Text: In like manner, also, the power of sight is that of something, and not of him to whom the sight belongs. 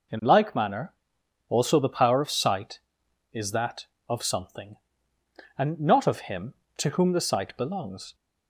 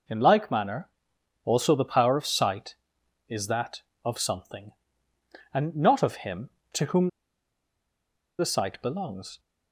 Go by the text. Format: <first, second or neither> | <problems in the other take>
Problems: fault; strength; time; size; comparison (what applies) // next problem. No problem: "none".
first | pauses between "whom" and "the"; strong; at 7.0 s; 1.3 s long